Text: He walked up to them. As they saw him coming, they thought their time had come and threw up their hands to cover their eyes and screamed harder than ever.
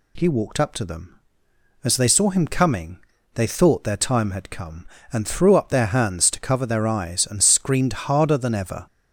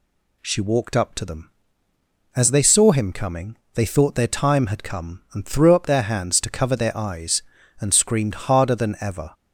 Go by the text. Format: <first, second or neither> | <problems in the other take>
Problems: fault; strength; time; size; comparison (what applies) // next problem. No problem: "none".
first | says "She" for "He"; at 0.4 s